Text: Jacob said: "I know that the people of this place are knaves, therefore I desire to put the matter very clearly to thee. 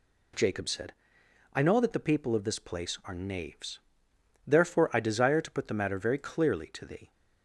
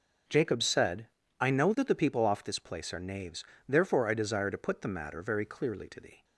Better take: first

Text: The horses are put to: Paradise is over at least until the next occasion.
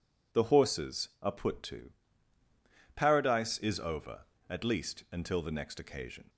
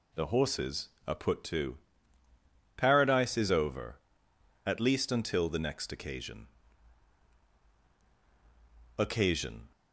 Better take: first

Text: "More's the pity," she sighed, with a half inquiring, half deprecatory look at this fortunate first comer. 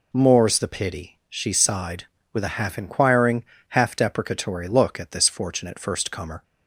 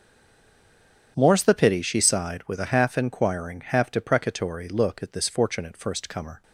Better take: first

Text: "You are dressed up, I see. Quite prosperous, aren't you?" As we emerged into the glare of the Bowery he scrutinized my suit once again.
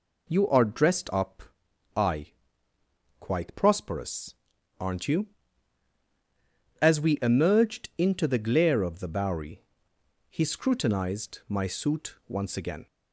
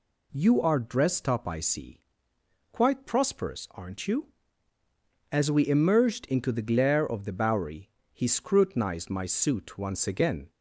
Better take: second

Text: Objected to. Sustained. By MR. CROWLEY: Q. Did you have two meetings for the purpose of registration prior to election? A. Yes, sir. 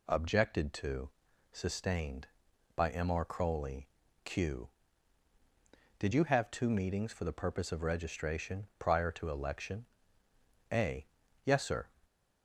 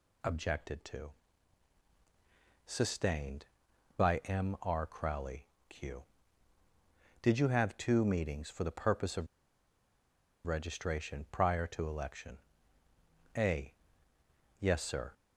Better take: first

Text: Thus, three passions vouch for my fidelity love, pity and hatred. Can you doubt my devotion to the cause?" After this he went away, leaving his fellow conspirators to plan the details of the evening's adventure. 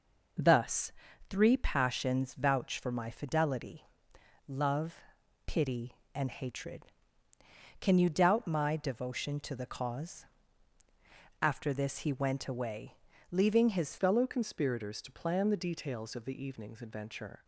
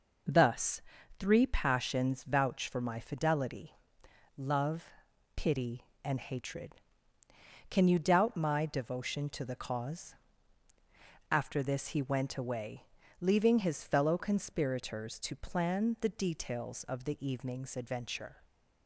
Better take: second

